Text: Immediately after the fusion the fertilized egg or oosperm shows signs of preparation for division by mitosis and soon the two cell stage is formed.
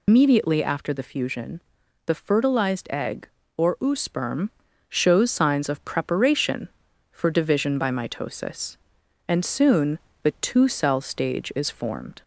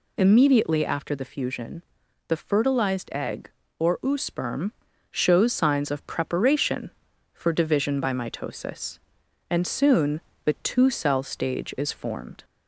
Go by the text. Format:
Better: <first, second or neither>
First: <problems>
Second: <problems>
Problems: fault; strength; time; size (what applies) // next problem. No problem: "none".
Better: second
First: loses the start of "Immediately"; at 0.0 s; 120 ms // pauses between "fusion" and "the"; noticeable; at 1.6 s; 0.46 s long // pauses between "oosperm" and "shows"; at 4.4 s; 0.40 s long // pauses between "soon" and "the"; slight; at 9.9 s; 0.24 s long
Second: pauses between "fusion" and "the"; noticeable; at 1.8 s; 0.46 s long // pauses between "oosperm" and "shows"; at 4.7 s; 0.40 s long // pauses between "soon" and "the"; slight; at 10.2 s; 0.24 s long